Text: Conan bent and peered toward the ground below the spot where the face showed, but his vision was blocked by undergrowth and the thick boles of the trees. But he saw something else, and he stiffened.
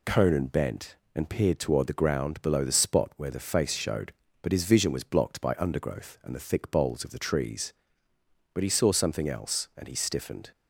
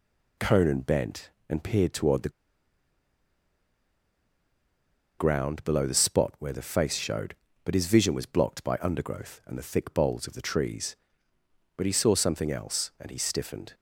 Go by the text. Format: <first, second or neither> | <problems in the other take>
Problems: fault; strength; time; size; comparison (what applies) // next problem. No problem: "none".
first | pauses between "the" and "ground"; strong; at 2.2 s; 2.8 s long